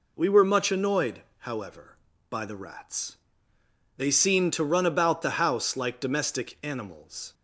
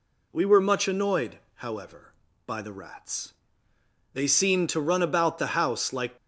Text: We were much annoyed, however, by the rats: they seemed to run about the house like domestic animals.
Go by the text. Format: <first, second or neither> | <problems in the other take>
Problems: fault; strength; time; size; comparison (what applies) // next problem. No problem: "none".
first | stops before "domestic animals"; at 6.1 s